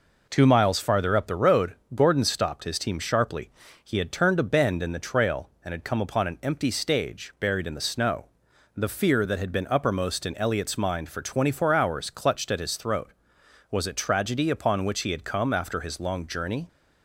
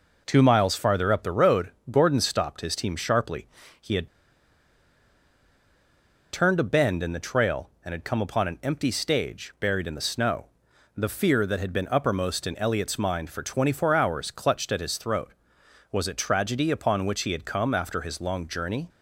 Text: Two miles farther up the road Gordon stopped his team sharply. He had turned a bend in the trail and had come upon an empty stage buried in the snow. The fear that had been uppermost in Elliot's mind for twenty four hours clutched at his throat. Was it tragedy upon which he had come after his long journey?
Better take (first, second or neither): first